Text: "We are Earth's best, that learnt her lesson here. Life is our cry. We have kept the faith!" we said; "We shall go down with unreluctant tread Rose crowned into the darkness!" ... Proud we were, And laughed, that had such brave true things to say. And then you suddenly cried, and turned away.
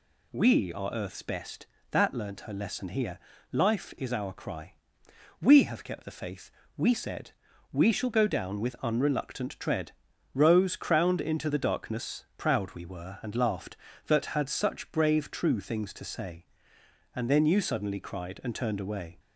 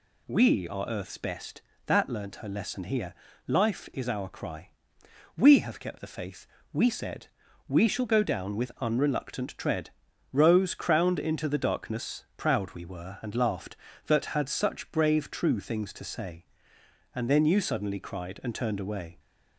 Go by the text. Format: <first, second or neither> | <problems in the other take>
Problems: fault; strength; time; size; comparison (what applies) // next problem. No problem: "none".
neither | pauses between "tread" and "Rose"; the same in both